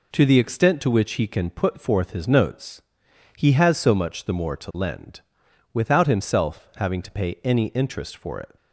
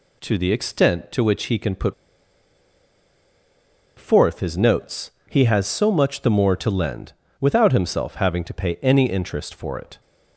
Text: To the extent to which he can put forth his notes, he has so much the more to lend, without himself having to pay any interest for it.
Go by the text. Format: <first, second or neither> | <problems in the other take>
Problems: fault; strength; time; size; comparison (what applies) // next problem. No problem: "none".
first | pauses between "put" and "forth"; strong; at 1.9 s; 2.0 s long